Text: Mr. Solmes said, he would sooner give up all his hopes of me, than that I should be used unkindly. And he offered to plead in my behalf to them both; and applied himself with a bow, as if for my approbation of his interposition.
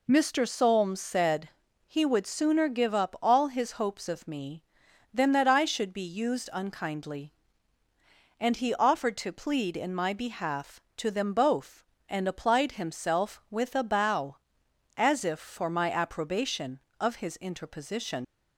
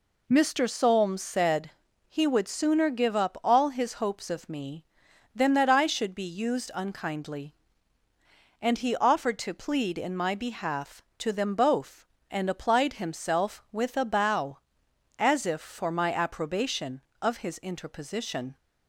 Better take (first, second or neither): second